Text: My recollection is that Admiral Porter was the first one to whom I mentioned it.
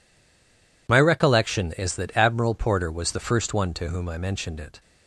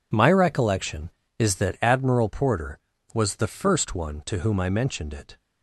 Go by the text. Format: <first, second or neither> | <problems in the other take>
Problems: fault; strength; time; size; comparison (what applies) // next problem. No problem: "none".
second | stays silent before the first word; slight; until 0.8 s; 0.8 s long